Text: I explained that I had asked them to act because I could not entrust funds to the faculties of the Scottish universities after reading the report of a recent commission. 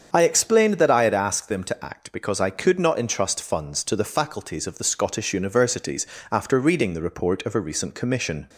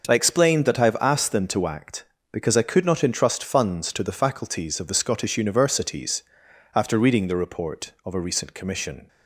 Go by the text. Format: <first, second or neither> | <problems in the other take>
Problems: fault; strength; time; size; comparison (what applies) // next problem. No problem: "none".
first | starts louder than the rest; until 1.1 s; 6.5 dB; strong in the first // says "have" for "had"; at 0.8 s // pauses between "universities" and "after"; noticeable; at 6.2 s; 0.54 s long; slight in the first